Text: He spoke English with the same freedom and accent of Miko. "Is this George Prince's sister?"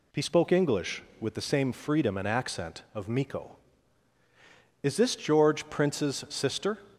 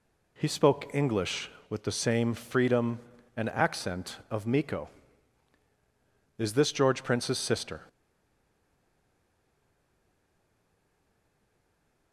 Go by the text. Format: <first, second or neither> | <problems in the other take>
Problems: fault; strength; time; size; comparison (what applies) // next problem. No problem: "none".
first | stays silent after the last word; strong; from 7.8 s on; 4.3 s long